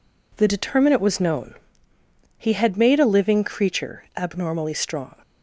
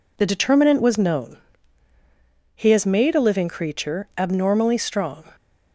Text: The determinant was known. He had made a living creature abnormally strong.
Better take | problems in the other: first | says "has" for "had"; at 2.7 s

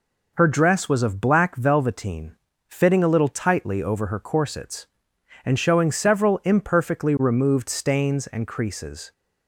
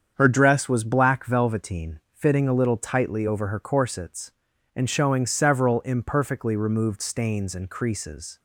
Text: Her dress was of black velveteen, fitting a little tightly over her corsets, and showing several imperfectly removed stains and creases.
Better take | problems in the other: first | starts louder than the rest; strong; until 1.1 s; 7.5 dB // skips "of"; at 0.8 s

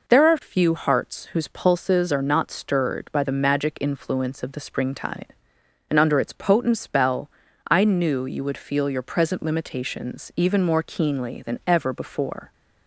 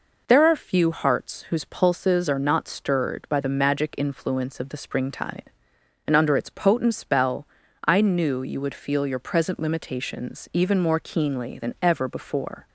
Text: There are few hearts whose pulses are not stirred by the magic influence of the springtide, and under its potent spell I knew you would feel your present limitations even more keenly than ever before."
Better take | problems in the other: neither | pauses between "spell" and "I"; the same in both

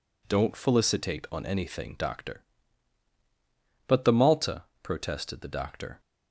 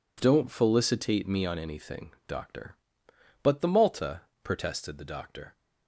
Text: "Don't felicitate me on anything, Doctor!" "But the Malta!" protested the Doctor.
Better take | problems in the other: second | skips "me"; at 1.2 s

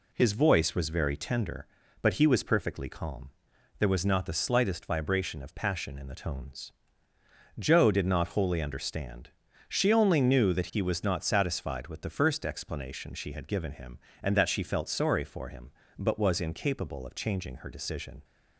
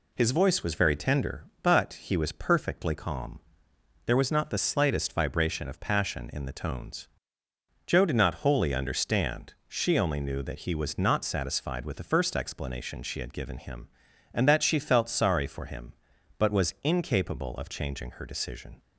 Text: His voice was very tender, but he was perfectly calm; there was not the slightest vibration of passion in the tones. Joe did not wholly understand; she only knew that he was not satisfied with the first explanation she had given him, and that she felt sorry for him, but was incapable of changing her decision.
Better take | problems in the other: neither | none

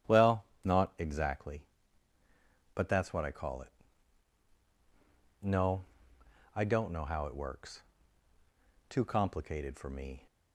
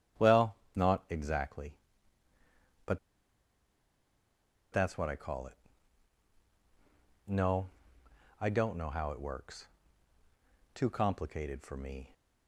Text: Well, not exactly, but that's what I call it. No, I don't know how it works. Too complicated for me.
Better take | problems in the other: first | starts louder than the rest; strong; until 1.4 s; 10.5 dB; strong in the first // pauses between "but" and "that's"; strong; at 2.9 s; 1.7 s long

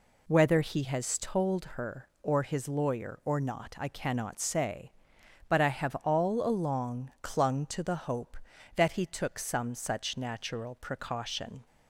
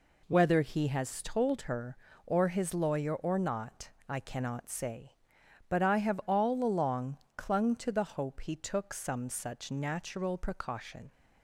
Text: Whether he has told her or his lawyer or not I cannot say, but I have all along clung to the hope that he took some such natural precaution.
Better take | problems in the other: first | pauses between "not" and "I"; slight; at 3.9 s; 0.17 s long // pauses between "along" and "clung"; slight; at 7.1 s; 0.18 s long // skips "that"; at 8.4 s

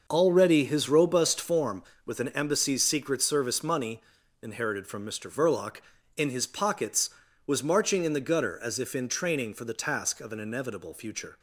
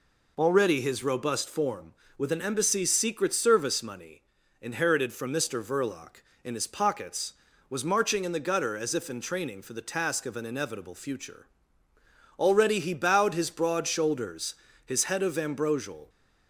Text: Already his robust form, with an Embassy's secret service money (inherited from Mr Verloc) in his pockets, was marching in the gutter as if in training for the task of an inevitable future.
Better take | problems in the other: first | goes on to say "Already he bowed his broad shoulders his head of ambrosial"; strong; from 12.3 s on; 3.7 s long

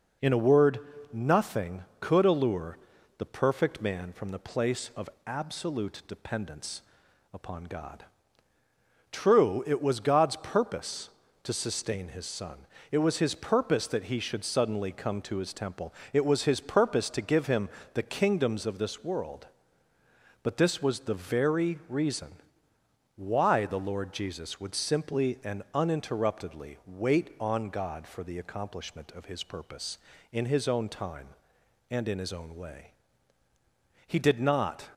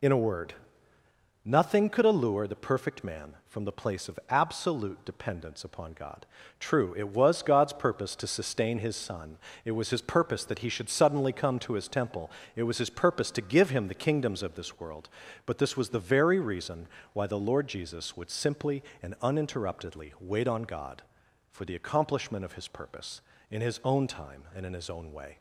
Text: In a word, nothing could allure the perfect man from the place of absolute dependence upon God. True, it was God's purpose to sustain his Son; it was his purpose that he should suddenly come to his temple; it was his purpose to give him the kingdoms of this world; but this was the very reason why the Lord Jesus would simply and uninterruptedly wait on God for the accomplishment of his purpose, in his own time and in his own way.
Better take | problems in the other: second | pauses between "allure" and "the"; at 2.7 s; 0.40 s long // pauses between "of" and "absolute"; slight; at 5.0 s; 0.16 s long // pauses between "dependence" and "upon"; noticeable; at 6.8 s; 0.52 s long // pauses between "him" and "the"; slight; at 17.6 s; 0.24 s long // pauses between "reason" and "why"; noticeable; at 22.3 s; 0.82 s long; slight in the second // goes on to say "He did not"; noticeable; from 34.0 s on; 0.84 s long

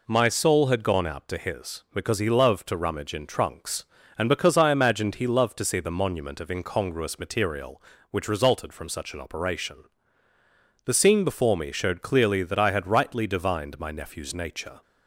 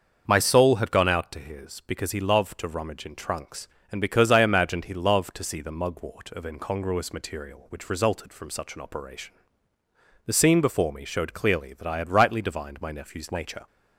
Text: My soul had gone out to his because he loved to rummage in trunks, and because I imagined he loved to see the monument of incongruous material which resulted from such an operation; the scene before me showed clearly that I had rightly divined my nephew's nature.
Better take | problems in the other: first | starts louder than the rest; until 1.2 s; 6.5 dB // says "mugwort" for "monument"; at 5.7 s

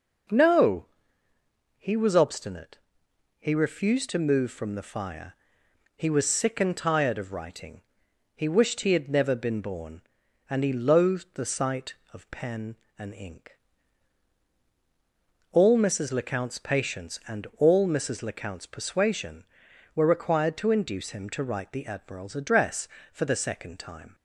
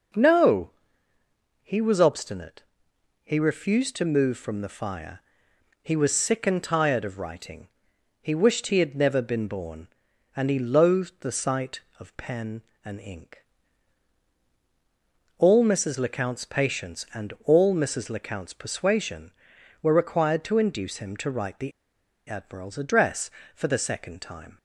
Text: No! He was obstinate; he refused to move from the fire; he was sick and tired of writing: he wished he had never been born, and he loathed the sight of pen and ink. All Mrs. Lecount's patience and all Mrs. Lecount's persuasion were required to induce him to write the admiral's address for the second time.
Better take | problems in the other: first | pauses between "the" and "admiral's"; noticeable; at 21.7 s; 0.55 s long

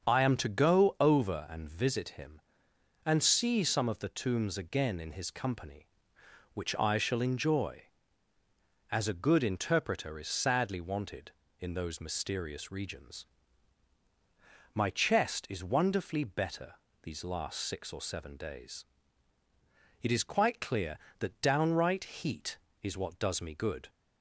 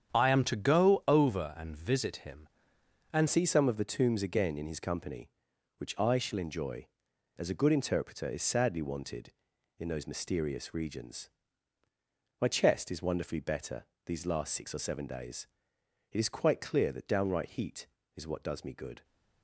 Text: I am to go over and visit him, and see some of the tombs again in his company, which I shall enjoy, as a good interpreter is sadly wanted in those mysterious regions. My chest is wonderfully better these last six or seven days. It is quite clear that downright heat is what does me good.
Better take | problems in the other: first | starts louder than the rest; strong; until 1.1 s; 8.5 dB; also in the first // changes voice at "see"; from 3.2 s on; 15.8 s long // pauses between "better" and "these"; slight; at 13.8 s; 0.22 s long; slight in the first

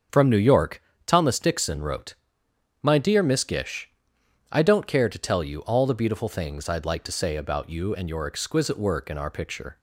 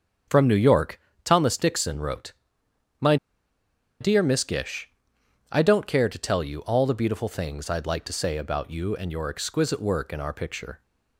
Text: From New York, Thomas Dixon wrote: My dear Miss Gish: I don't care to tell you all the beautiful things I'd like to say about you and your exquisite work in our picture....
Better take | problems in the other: first | starts louder than the rest; until 1.5 s; 7 dB; also in the first // pauses between "My" and "dear"; noticeable; at 3.1 s; 0.84 s long

